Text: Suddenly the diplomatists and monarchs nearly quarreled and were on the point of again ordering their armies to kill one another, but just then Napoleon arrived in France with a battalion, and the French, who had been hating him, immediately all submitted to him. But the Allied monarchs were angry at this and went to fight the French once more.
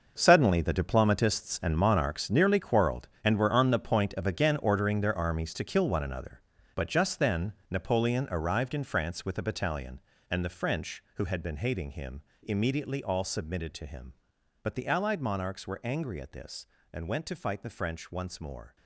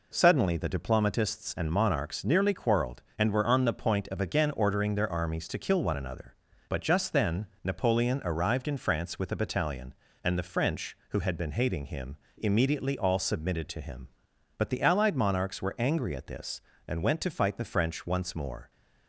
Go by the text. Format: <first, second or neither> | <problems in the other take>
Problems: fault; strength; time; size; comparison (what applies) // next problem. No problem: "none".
second | gets quieter; strong; throughout; 13 dB // pauses between "then" and "Napoleon"; slight; at 7.5 s; 0.16 s long; slight in the second